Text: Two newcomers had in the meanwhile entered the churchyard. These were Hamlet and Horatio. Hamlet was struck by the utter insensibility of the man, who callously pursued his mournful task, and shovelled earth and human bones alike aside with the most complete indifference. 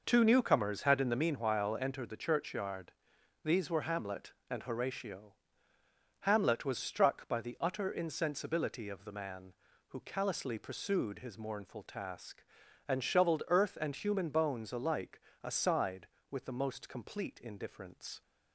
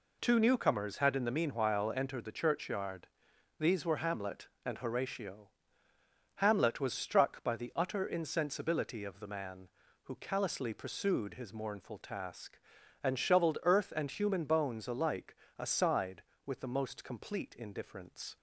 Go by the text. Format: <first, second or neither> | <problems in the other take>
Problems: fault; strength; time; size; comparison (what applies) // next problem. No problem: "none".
second | starts louder than the rest; noticeable; until 1.4 s; 5.5 dB // pauses between "alike" and "aside"; slight; at 15.2 s; 0.20 s long; slight in the second